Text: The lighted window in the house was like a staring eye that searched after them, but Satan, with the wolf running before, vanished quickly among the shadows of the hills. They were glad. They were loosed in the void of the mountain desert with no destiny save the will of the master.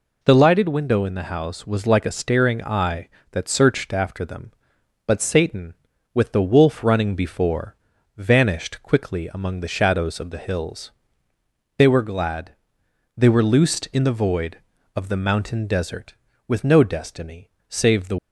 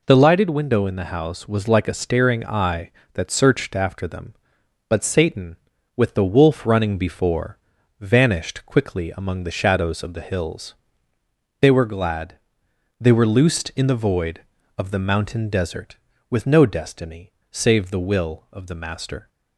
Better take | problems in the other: second | pauses between "destiny" and "save"; slight; at 17.4 s; 0.22 s long; slight in the second // stops before "will of the master"; at 18.1 s

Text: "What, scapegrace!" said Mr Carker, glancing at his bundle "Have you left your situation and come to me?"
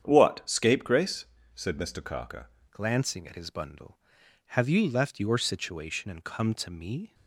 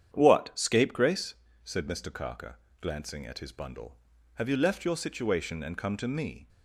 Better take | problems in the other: second | starts louder than the rest; strong; until 1.0 s; 8.5 dB; strong in the second // changes voice at "glancing"; from 2.7 s on; 4.4 s long

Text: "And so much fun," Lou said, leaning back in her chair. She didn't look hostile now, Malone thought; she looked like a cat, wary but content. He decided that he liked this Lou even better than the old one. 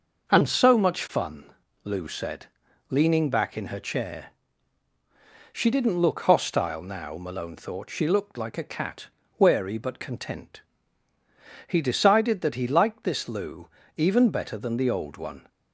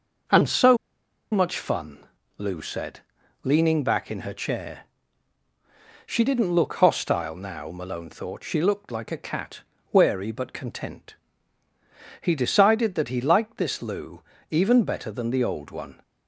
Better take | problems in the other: first | starts louder than the rest; noticeable; until 1.8 s; 6 dB; noticeable in the first // pauses between "so" and "much"; noticeable; at 0.7 s; 0.54 s long // pauses between "Lou" and "even"; slight; at 14.2 s; 0.28 s long; slight in the first

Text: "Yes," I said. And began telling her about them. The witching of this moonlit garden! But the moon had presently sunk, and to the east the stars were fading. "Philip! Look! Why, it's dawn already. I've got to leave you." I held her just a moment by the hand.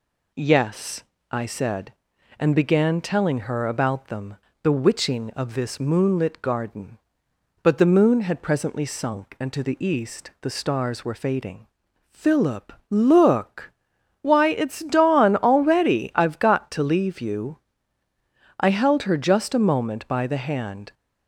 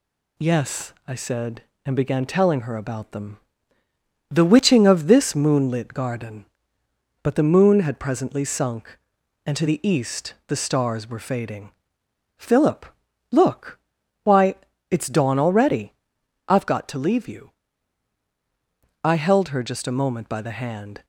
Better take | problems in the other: neither | none

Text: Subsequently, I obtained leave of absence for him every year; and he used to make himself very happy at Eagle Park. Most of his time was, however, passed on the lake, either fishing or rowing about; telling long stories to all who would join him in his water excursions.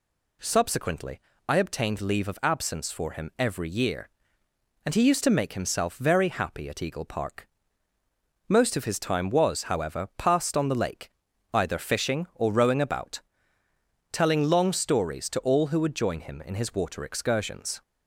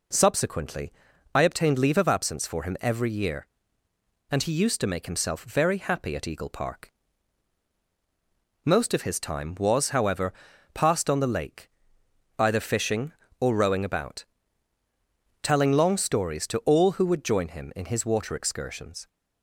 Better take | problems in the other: neither | none

